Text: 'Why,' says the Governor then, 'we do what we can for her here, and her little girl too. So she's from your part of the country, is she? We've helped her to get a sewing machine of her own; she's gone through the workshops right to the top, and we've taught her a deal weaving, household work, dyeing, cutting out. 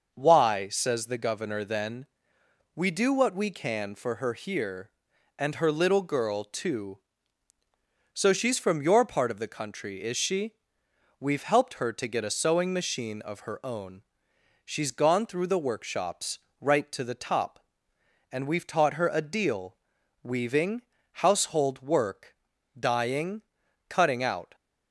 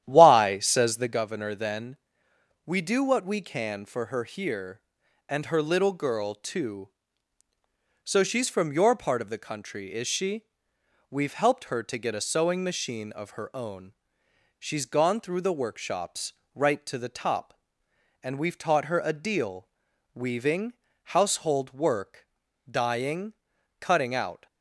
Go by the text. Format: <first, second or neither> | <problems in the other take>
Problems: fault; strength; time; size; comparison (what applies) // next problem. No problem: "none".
first | starts louder than the rest; strong; until 1.3 s; 11 dB // pauses between "workshops" and "right"; slight; at 16.3 s; 0.20 s long; slight in the first // pauses between "deal" and "weaving"; noticeable; at 19.6 s; 0.46 s long; noticeable in the first